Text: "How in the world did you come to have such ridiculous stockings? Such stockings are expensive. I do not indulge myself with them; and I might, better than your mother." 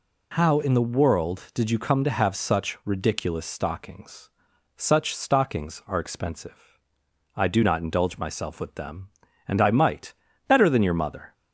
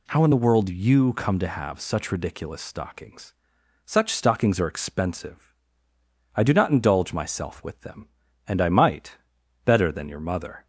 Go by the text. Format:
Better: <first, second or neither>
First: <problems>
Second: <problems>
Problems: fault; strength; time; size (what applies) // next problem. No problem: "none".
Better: first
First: none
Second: skips "did"; at 0.6 s